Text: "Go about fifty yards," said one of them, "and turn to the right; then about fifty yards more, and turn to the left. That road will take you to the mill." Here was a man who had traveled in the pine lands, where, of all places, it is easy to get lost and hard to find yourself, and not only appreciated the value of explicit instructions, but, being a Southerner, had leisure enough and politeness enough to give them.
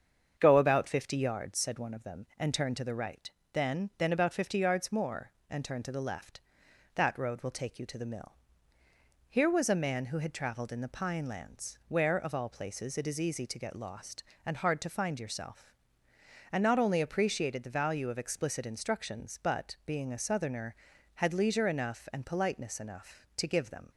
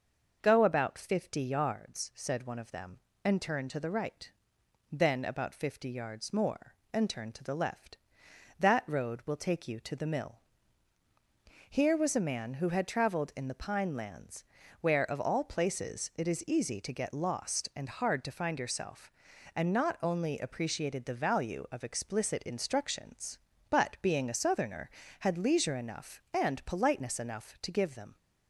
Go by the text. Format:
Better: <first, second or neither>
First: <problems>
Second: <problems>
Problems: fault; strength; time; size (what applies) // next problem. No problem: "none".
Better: second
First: starts louder than the rest; strong; until 1.3 s; 7.5 dB // says "then" twice; at 3.9 s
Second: starts louder than the rest; noticeable; until 1.4 s; 6 dB